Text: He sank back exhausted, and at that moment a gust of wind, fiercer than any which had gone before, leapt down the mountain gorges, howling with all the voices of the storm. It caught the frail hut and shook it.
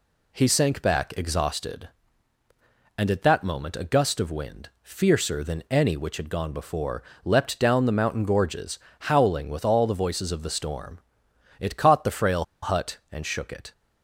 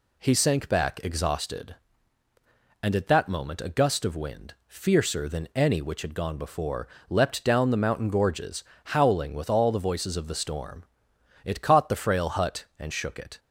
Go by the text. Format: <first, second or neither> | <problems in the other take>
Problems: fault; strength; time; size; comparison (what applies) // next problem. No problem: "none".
second | pauses between "frail" and "hut"; slight; at 12.4 s; 0.17 s long